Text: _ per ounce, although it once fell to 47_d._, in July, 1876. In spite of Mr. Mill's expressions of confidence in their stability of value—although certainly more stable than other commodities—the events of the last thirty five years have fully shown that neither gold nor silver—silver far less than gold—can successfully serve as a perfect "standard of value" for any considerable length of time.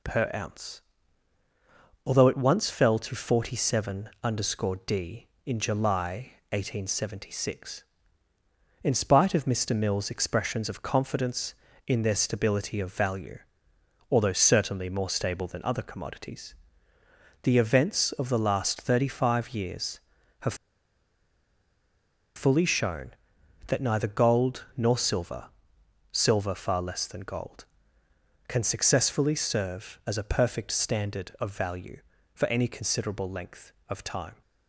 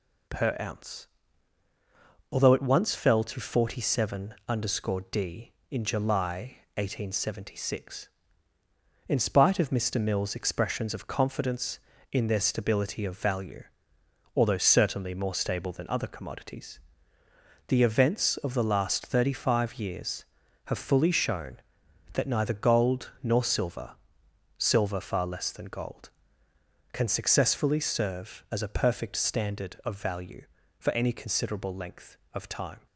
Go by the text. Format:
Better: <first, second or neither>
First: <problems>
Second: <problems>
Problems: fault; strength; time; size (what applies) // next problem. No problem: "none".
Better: second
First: pauses between "have" and "fully"; strong; at 20.5 s; 1.8 s long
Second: none